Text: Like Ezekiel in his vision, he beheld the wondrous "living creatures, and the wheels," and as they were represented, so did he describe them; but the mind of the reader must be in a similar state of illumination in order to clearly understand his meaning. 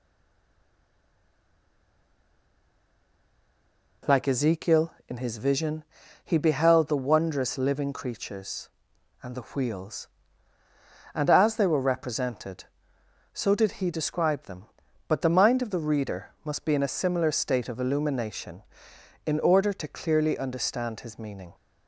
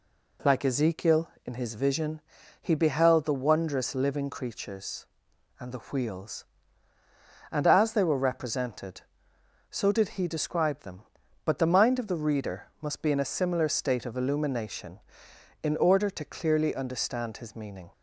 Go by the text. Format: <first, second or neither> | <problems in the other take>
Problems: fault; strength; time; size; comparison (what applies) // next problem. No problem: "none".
second | stays silent before the first word; strong; until 4.0 s; 4.0 s long